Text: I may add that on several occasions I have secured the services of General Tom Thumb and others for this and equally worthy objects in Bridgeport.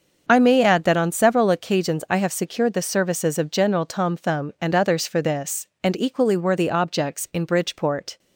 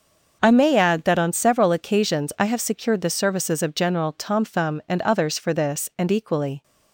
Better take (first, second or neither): first